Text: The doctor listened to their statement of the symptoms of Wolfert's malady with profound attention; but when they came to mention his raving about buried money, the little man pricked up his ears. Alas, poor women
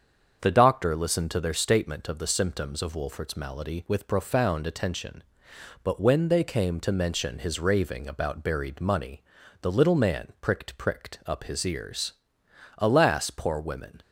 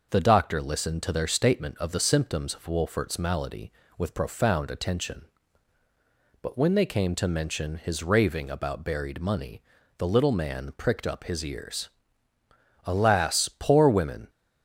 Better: second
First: starts louder than the rest; until 1.4 s; 7 dB // says "pricked" twice; at 10.7 s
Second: none

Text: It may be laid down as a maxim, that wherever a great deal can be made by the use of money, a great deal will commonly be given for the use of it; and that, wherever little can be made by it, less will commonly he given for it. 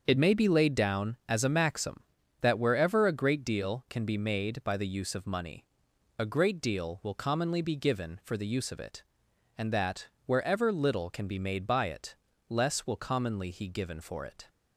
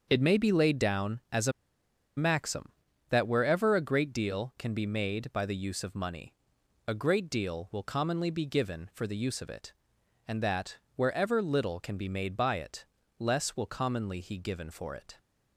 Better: first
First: starts louder than the rest; until 1.1 s; 6.5 dB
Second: starts louder than the rest; until 1.1 s; 7 dB // pauses between "a" and "maxim"; noticeable; at 1.5 s; 0.65 s long

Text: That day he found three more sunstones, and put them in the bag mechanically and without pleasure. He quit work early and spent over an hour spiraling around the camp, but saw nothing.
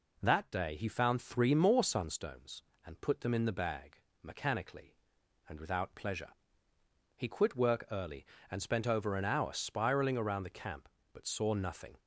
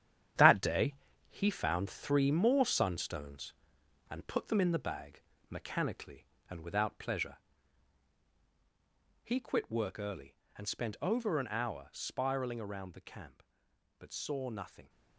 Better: first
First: pauses between "bag" and "mechanically"; slight; at 4.0 s; 0.22 s long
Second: gets quieter; strong; throughout; 8.5 dB // pauses between "day" and "he"; slight; at 0.9 s; 0.36 s long // pauses between "bag" and "mechanically"; slight; at 5.2 s; 0.28 s long

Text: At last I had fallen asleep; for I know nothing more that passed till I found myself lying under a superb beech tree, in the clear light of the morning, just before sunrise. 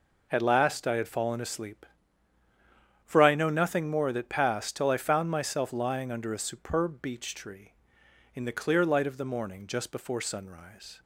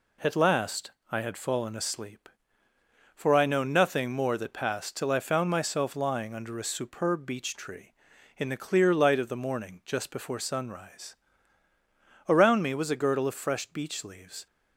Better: first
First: none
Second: pauses between "last" and "I"; slight; at 0.9 s; 0.20 s long // goes on to say "Around me was a girdle of fresh beech leaves"; strong; from 12.2 s on; 2.1 s long

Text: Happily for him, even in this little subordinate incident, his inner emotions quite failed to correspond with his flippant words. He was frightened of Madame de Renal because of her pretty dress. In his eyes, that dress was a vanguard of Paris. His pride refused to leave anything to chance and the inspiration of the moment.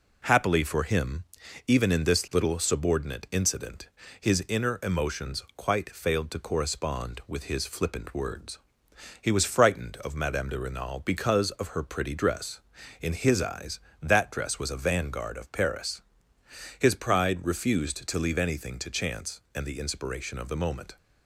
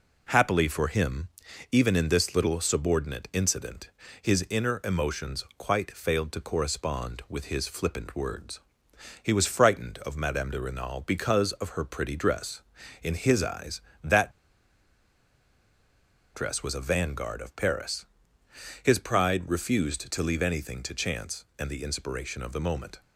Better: first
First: none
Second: pauses between "that" and "dress"; strong; at 14.3 s; 2.0 s long

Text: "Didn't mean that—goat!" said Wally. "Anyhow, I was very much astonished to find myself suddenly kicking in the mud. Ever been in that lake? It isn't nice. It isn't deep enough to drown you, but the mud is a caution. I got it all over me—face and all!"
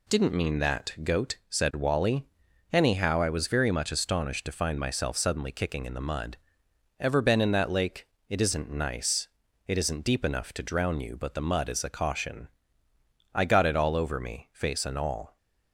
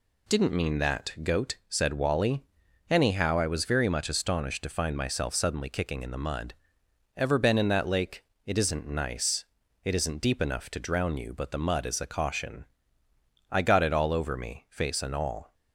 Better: neither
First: none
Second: none

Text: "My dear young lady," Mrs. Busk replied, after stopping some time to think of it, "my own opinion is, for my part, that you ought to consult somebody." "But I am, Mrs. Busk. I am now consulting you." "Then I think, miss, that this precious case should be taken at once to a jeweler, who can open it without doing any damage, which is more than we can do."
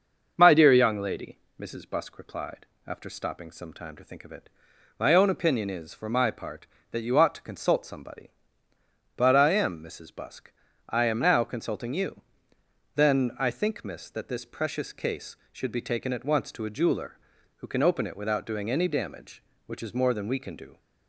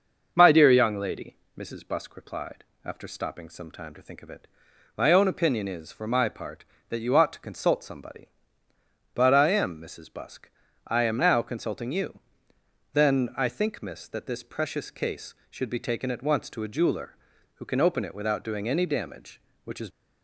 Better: first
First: starts louder than the rest; until 1.3 s; 6 dB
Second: starts louder than the rest; until 1.3 s; 6 dB // stops before "more than we can do"; at 19.9 s

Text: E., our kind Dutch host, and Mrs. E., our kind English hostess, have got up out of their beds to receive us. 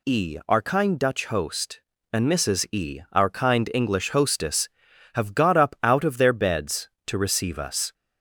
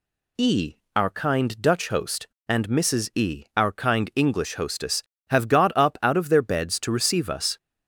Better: neither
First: none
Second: none

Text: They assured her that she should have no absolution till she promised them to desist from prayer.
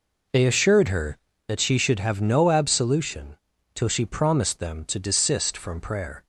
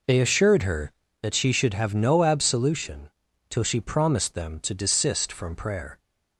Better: neither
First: pauses between "absolution" and "till"; at 3.3 s; 0.38 s long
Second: pauses between "absolution" and "till"; at 3.0 s; 0.40 s long

